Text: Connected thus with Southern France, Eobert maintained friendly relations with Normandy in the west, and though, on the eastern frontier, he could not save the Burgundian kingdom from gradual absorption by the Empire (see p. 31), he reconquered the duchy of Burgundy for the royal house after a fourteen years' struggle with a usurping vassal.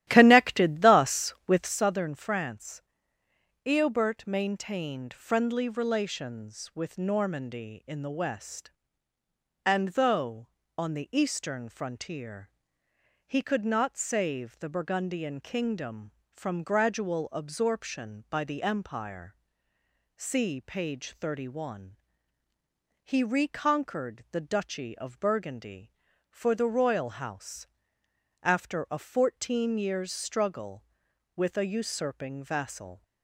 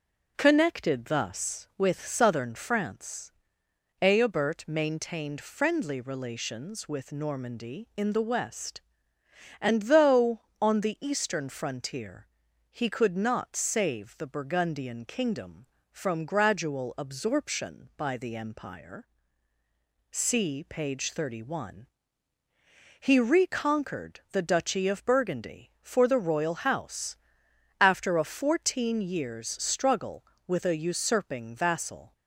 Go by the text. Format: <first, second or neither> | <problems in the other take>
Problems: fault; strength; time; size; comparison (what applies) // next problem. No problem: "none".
second | starts louder than the rest; strong; until 1.8 s; 13.5 dB // pauses between "house" and "after"; noticeable; at 27.6 s; 0.74 s long; noticeable in the second